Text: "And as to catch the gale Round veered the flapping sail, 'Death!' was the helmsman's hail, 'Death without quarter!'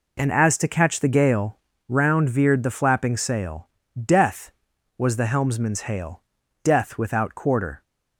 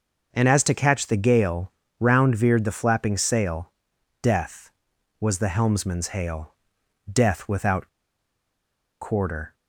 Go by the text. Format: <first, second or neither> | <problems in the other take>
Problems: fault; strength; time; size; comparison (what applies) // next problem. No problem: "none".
first | starts louder than the rest; noticeable; until 1.3 s; 6 dB // pauses between "gale" and "Round"; slight; at 1.7 s; 0.26 s long; slight in the first // pauses between "without" and "quarter"; at 7.8 s; 1.1 s long